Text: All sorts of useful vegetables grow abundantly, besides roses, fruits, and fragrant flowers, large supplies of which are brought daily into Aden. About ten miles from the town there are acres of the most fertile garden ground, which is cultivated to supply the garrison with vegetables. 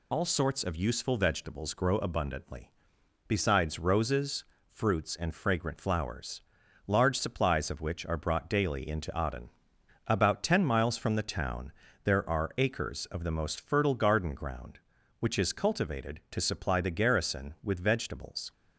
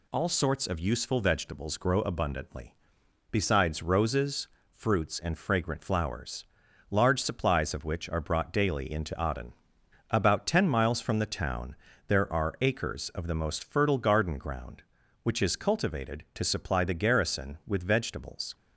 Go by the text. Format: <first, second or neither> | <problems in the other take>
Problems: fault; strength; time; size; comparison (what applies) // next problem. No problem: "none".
second | loses the start of "All"; at 0.1 s; 50 ms // pauses between "town" and "there"; slight; at 11.7 s; 0.32 s long; slight in the second